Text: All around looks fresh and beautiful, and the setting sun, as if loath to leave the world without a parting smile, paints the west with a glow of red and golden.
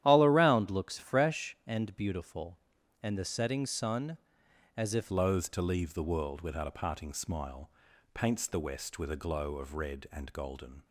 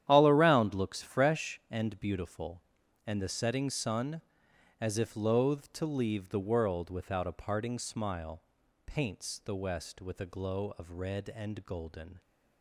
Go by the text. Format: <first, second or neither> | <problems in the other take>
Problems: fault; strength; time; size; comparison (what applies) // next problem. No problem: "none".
second | starts louder than the rest; strong; until 1.0 s; 11.5 dB; strong in the second // changes voice at "loath"; from 5.0 s on; 5.8 s long